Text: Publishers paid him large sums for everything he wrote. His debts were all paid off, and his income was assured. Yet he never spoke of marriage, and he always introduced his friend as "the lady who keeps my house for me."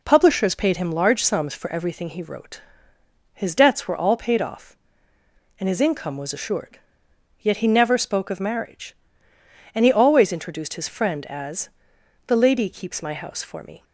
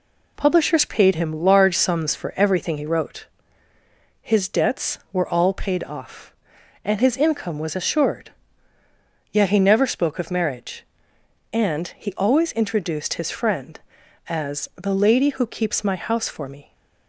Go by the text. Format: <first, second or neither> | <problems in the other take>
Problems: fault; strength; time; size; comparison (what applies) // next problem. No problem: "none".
second | pauses between "as" and "the"; noticeable; at 11.6 s; 0.56 s long // skips "who"; at 12.6 s